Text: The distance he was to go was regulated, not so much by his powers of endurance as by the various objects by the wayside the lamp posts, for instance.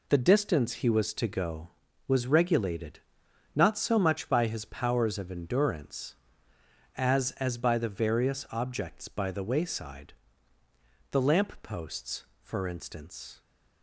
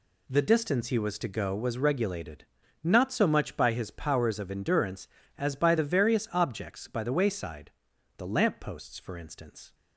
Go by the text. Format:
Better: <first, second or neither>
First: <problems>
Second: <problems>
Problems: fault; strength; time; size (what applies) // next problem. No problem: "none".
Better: second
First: says "as" twice; at 7.3 s // pauses between "wayside" and "the"; noticeable; at 10.1 s; 0.98 s long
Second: pauses between "wayside" and "the"; noticeable; at 7.7 s; 0.46 s long